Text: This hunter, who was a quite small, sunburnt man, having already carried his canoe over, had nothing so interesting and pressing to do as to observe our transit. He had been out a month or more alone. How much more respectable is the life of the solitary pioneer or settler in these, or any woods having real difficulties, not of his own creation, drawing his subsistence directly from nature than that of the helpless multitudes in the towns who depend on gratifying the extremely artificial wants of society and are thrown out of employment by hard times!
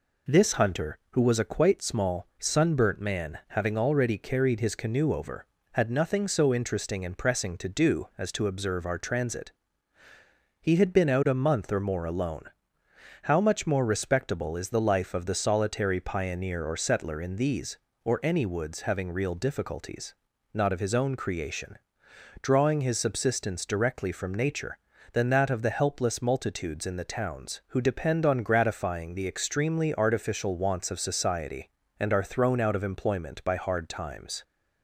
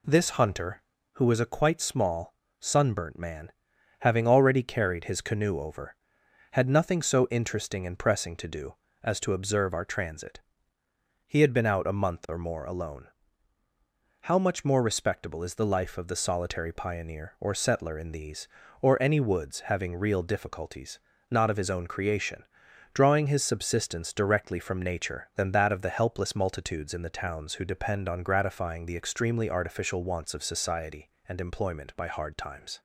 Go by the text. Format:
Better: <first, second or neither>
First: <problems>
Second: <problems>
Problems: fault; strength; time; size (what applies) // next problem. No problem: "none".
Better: first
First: none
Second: skips "are thrown out of"; at 31.4 s